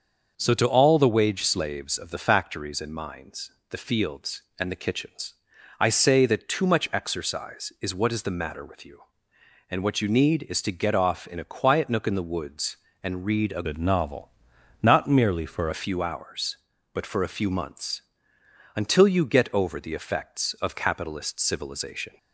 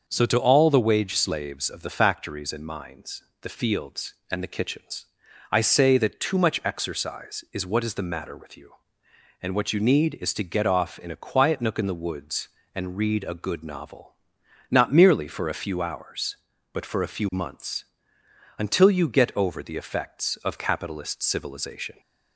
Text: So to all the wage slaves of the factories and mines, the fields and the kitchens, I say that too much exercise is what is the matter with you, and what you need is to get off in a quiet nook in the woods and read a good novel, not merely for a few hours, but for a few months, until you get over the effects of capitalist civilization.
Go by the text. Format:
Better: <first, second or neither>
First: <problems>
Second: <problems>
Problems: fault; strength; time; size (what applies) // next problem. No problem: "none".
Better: second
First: starts louder than the rest; until 1.3 s; 6.5 dB // changes voice from "good" to "for"; from 13.6 to 15.6 s; 2.0 s long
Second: starts louder than the rest; until 1.1 s; 6.5 dB